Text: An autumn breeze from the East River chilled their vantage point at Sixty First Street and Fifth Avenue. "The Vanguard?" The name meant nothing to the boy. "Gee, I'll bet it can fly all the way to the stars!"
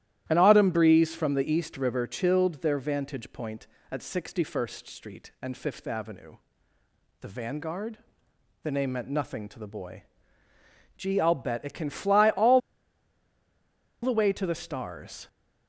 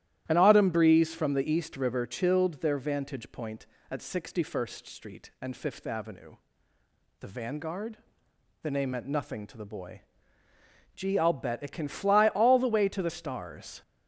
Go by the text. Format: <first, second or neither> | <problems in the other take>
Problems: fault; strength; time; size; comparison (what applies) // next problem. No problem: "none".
second | starts louder than the rest; strong; until 1.3 s; 12.5 dB; strong in the second // pauses between "all" and "the"; strong; at 12.5 s; 1.4 s long